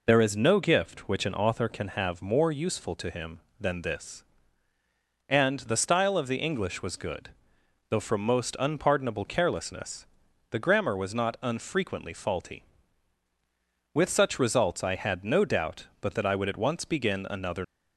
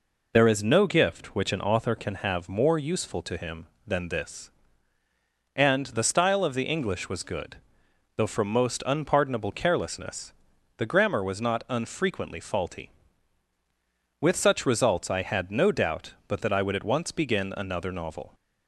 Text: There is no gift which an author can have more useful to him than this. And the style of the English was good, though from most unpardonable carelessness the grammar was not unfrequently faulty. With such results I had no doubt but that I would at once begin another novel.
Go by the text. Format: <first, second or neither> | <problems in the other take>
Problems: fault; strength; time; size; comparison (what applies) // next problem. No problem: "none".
second | pauses between "carelessness" and "the"; at 10.0 s; 0.44 s long; also in the second // stops before "novel"; at 17.6 s